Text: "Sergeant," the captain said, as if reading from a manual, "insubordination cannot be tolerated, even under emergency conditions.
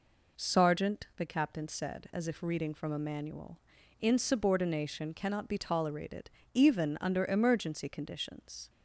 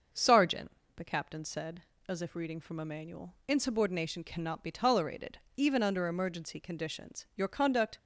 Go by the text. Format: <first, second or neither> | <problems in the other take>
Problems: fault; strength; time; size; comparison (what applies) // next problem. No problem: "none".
first | starts louder than the rest; until 1.4 s; 6 dB // goes on to say "Your conduct"; from 7.3 s on; 0.60 s long